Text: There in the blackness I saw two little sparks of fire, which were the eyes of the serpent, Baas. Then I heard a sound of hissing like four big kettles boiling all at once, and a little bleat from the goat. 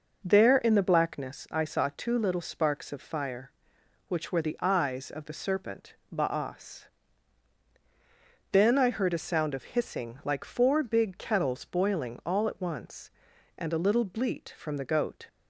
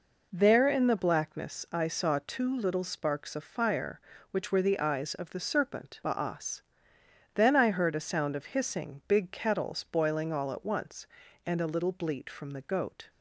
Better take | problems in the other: first | skips "like four"; at 9.0 s

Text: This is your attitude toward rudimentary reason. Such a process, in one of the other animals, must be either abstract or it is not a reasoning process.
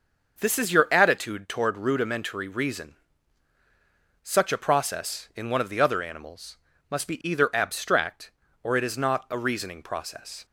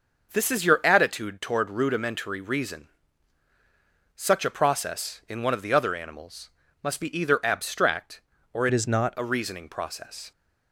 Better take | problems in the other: first | starts louder than the rest; noticeable; until 1.3 s; 6 dB; noticeable in the first // changes voice from "it" to "not"; from 8.7 to 9.1 s; 0.4 s long

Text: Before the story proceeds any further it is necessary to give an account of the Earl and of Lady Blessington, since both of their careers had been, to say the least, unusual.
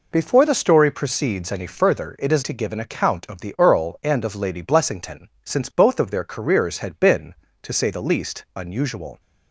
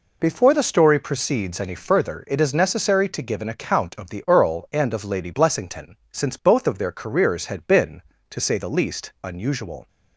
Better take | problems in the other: second | skips "necessary"; at 2.4 s

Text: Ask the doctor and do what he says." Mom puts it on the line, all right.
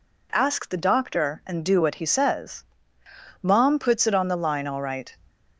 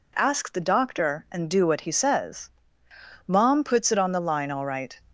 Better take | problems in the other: neither | none

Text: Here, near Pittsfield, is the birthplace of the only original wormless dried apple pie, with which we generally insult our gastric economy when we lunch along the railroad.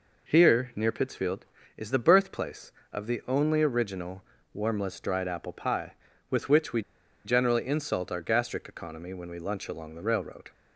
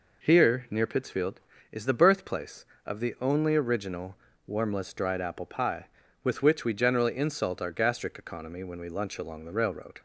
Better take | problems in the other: second | pauses between "original" and "wormless"; slight; at 4.2 s; 0.30 s long; slight in the second // pauses between "we" and "generally"; at 6.8 s; 0.43 s long

